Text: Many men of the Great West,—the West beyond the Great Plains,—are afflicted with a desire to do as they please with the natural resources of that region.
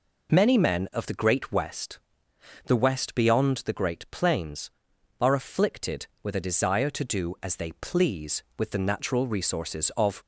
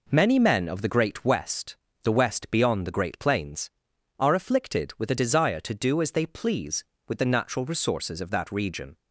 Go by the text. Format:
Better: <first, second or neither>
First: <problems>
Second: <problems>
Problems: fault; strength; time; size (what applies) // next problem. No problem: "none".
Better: second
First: stops before "that region"; at 10.2 s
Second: none